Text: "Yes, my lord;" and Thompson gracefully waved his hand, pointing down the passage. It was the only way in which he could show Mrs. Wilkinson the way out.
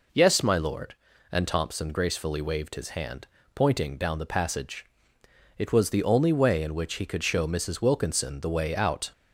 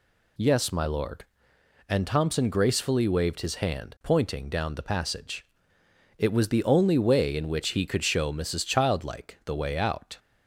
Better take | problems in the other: first | says "Childlike" for "Wilkinson"; at 8.6 s

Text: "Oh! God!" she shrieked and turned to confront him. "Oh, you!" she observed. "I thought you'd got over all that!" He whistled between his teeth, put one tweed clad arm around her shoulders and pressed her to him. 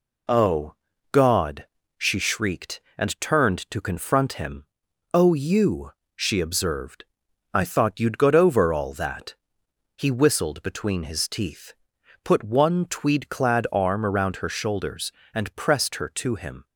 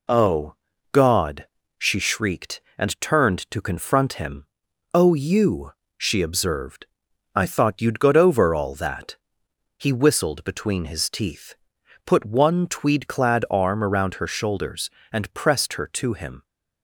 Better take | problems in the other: neither | none

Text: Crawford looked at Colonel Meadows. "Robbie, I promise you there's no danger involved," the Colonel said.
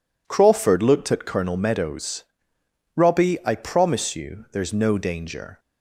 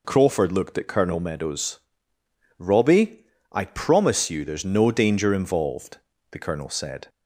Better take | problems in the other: second | stops before "involved the Colonel said"; at 5.5 s

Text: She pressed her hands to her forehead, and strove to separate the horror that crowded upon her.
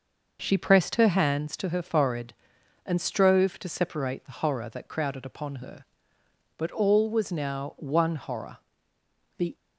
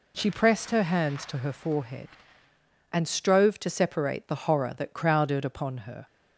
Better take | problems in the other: second | goes on to say "But all was now one horror the"; strong; from 6.5 s on; 2.9 s long

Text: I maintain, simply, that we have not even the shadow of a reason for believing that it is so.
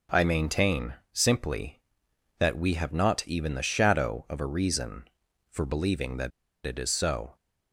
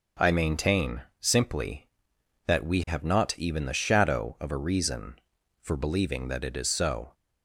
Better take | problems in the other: second | starts louder than the rest; until 1.3 s; 6 dB; also in the second // pauses between "that" and "it"; slight; at 6.3 s; 0.34 s long

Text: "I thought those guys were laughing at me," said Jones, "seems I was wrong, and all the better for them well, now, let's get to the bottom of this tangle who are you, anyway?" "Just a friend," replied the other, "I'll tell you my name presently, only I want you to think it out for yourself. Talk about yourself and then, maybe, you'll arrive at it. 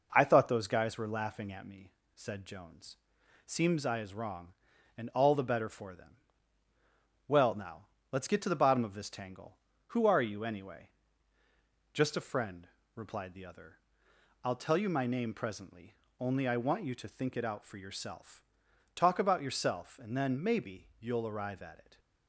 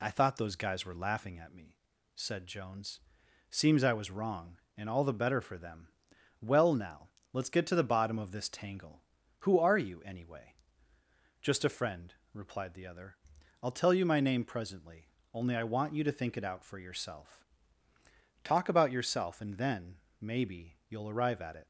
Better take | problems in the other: second | says "is" for "was"; at 4.0 s // pauses between "them" and "well"; at 6.1 s; 1.1 s long; noticeable in the second

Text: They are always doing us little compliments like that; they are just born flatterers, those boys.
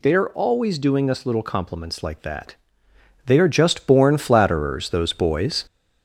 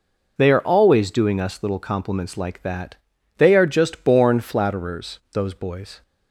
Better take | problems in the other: second | gets louder; throughout; 3.5 dB

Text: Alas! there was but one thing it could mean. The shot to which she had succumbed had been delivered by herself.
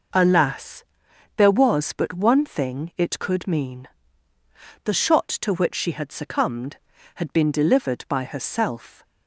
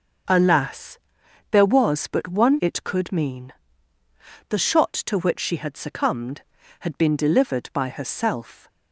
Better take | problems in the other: first | starts louder than the rest; until 1.8 s; 6.5 dB // skips "thing"; at 2.5 s

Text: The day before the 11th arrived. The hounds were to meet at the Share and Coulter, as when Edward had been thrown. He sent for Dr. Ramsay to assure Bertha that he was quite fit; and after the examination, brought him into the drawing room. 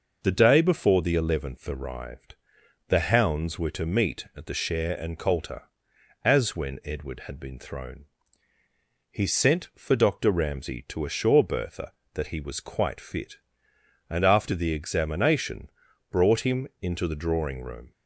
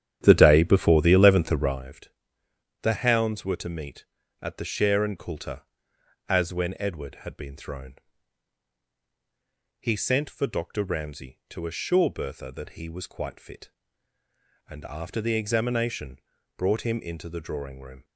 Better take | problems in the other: first | starts louder than the rest; strong; until 1.8 s; 10 dB

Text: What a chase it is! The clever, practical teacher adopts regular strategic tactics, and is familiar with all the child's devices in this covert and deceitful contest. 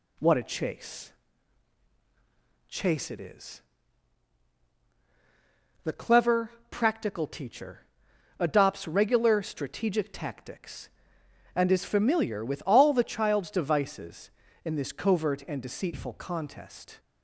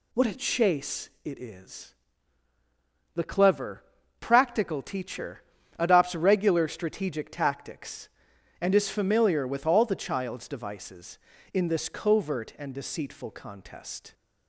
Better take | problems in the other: second | says "chase" twice; at 2.6 s // pauses between "teacher" and "adopts"; noticeable; at 7.8 s; 0.54 s long; also in the second

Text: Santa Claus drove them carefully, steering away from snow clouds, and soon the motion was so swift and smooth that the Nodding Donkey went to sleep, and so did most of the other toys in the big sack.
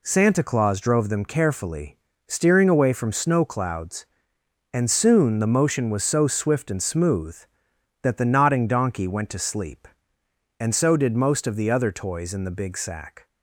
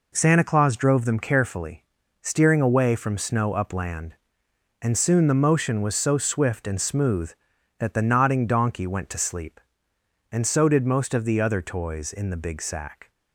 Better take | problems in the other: first | says "upland" for "clouds"; at 3.5 s

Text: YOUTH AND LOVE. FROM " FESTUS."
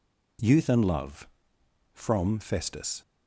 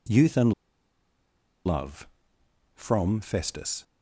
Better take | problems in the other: first | pauses between "AND" and "LOVE"; at 0.5 s; 1.1 s long

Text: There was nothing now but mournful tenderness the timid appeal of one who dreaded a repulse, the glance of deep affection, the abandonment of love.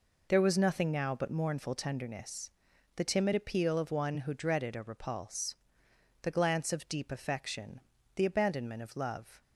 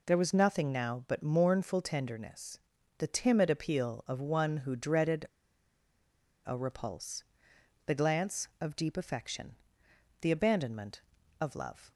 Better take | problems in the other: first | pauses between "tenderness" and "the"; at 2.5 s; 0.40 s long; noticeable in the first // pauses between "dreaded" and "a"; at 5.2 s; 1.2 s long

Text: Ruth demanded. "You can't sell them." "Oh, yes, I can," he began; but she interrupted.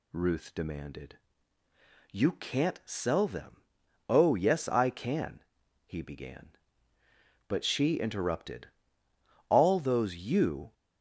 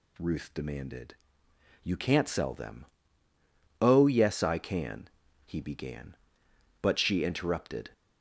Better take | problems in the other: second | goes on to say "All those you"; noticeable; from 9.4 s on; 1.2 s long

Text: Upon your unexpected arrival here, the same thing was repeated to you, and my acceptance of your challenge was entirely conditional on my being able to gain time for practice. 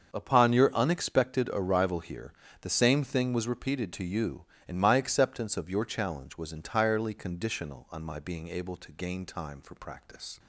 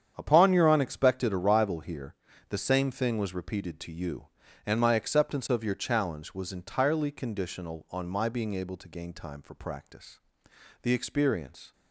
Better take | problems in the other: first | starts louder than the rest; strong; until 1.1 s; 8.5 dB; also in the first // goes on to say "The experience"; noticeable; from 10.8 s on; 0.90 s long

